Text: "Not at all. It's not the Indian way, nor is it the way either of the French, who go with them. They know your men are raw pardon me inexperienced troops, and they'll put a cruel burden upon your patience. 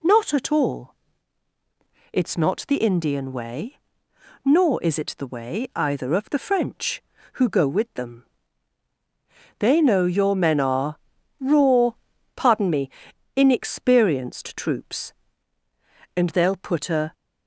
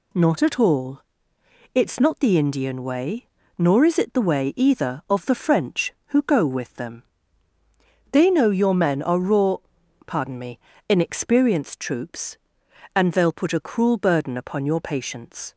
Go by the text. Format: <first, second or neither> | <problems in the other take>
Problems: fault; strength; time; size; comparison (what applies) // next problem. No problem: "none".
second | pauses between "are" and "raw"; at 10.9 s; 0.42 s long // pauses between "raw" and "pardon"; at 11.9 s; 0.44 s long; noticeable in the second // pauses between "me" and "inexperienced"; noticeable; at 12.8 s; 0.46 s long; slight in the second // stops before "cruel burden upon your patience"; at 17.1 s